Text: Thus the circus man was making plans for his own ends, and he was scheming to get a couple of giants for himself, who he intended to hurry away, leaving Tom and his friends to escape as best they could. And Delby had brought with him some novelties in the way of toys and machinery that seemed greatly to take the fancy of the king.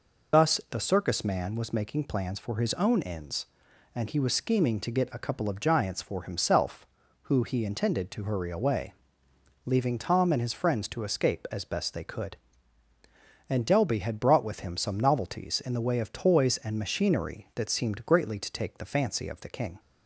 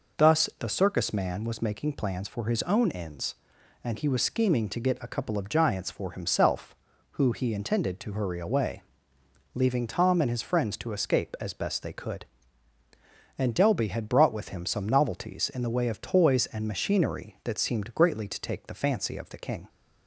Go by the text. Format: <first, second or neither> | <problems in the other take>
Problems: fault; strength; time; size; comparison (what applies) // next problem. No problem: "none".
second | loses the start of "Thus"; at 0.3 s; 40 ms